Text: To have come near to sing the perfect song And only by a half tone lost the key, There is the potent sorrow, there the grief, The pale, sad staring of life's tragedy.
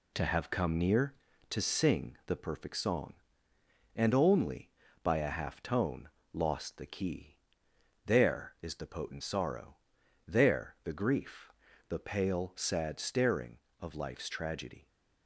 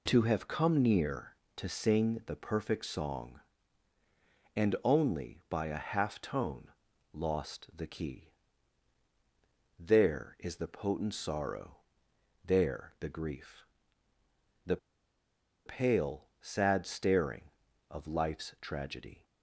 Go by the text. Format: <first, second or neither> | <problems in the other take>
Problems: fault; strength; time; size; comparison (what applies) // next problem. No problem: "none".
first | pauses between "tone" and "lost"; at 6.6 s; 0.44 s long; slight in the first // pauses between "The" and "pale"; noticeable; at 14.7 s; 0.89 s long